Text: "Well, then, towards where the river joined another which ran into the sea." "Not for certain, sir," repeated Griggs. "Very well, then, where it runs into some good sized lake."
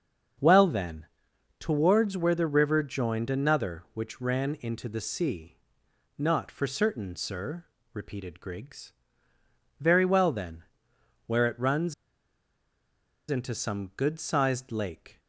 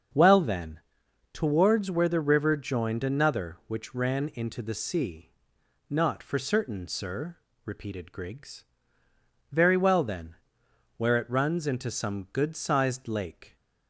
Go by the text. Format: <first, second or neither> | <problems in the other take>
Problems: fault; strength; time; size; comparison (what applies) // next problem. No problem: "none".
second | starts louder than the rest; until 1.9 s; 6.5 dB; also in the second // pauses between "runs" and "into"; strong; at 11.9 s; 1.3 s long